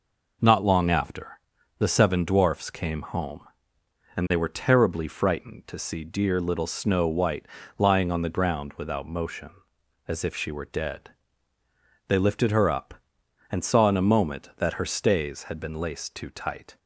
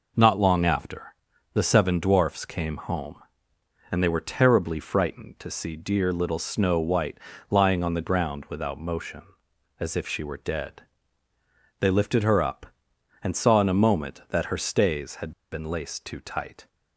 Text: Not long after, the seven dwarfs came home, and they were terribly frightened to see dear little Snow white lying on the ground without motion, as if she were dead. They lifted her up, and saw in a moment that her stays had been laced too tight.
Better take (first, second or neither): first